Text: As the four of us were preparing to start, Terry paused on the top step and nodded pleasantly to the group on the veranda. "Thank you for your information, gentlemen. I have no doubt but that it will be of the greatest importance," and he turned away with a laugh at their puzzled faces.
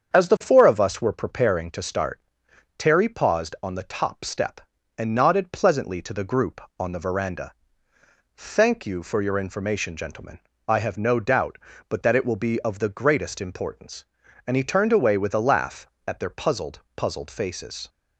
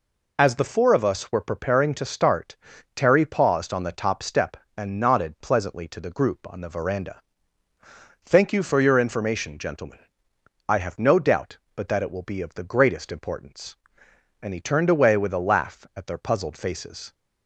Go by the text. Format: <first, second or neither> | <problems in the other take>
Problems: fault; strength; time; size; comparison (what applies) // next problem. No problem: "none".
second | starts louder than the rest; strong; until 1.1 s; 7.5 dB // says "puzzled" twice; at 16.9 s